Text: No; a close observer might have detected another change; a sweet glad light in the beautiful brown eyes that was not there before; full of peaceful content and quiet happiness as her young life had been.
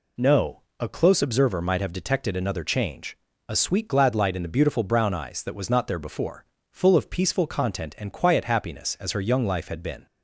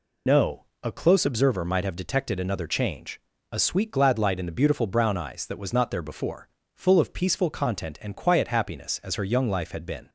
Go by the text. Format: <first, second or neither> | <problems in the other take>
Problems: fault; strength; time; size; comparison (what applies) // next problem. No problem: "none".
first | loses the start of "No"; at 0.2 s; 50 ms